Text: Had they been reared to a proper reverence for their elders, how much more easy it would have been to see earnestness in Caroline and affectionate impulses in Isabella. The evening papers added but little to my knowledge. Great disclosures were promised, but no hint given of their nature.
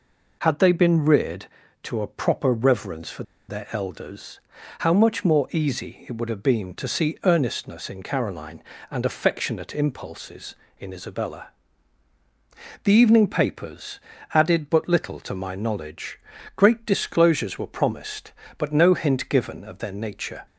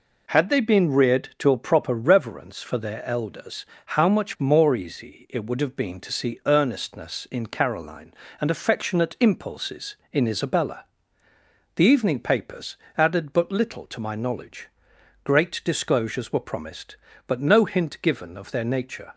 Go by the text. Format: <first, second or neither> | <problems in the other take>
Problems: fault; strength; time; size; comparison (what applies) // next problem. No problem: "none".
second | pauses between "for" and "their"; slight; at 3.2 s; 0.24 s long // pauses between "papers" and "added"; at 13.9 s; 0.38 s long; slight in the second